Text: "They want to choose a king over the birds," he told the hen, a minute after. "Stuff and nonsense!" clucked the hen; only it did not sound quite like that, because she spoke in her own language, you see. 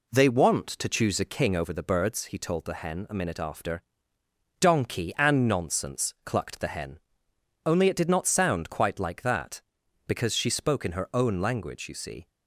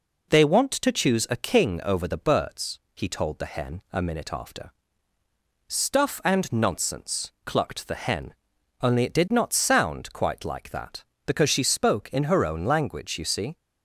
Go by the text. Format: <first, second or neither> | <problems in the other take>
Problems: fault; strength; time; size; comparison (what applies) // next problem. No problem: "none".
second | says "Donkey" for "Stuff"; at 4.6 s